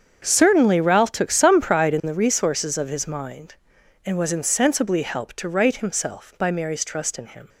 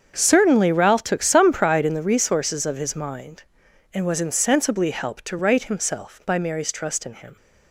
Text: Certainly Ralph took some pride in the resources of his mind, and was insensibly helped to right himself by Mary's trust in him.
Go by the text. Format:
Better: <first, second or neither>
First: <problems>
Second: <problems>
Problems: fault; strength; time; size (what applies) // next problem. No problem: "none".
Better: neither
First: starts louder than the rest; strong; until 1.2 s; 7 dB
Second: starts louder than the rest; strong; until 1.1 s; 7 dB